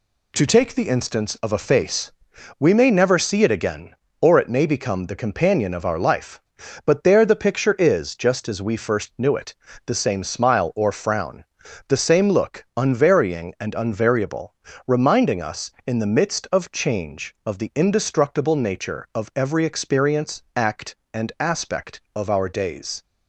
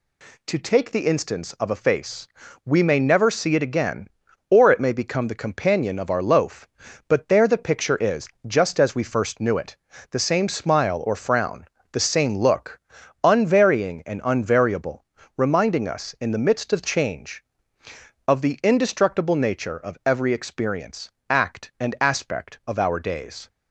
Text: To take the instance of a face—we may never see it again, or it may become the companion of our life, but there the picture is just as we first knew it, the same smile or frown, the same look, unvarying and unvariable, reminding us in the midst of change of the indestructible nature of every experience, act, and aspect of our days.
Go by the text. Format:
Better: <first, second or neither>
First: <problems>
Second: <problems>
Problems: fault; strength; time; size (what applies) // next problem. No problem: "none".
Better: first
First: none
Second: says "loaf" for "life"; at 6.2 s // pauses between "is" and "just"; slight; at 8.2 s; 0.18 s long